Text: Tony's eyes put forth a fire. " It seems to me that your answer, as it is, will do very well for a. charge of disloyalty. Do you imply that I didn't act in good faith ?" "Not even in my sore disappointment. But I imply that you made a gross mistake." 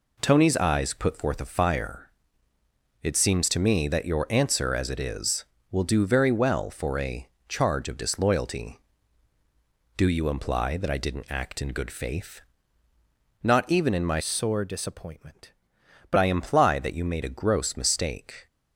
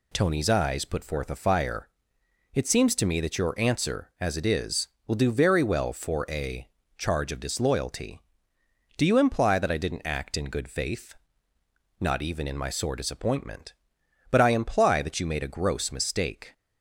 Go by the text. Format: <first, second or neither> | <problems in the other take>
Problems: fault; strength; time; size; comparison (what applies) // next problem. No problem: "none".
second | changes voice from "sore" to "But"; from 14.1 to 16.1 s; 2.0 s long